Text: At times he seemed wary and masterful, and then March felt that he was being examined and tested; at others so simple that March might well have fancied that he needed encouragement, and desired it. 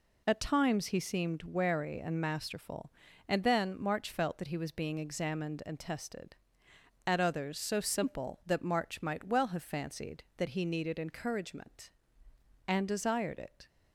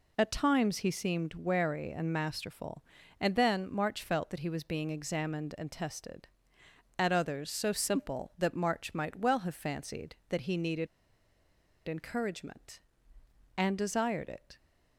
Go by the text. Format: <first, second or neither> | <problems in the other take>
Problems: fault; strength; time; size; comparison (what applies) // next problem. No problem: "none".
first | pauses between "needed" and "encouragement"; at 10.8 s; 1.0 s long